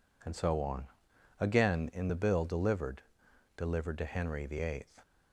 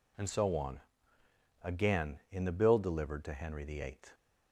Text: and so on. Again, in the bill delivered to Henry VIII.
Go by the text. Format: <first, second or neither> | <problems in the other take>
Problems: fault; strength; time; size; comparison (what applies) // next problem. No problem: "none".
second | says "delivered" twice; at 3.5 s